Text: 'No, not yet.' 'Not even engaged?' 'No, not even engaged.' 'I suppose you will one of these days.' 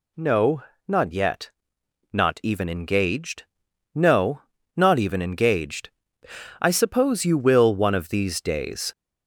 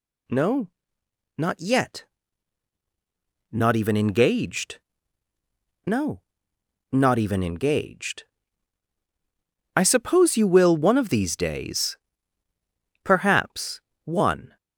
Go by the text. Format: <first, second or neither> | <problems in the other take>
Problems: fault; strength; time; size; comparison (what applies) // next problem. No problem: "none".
first | goes on to say "Perhaps one"; from 13.0 s on; 1.5 s long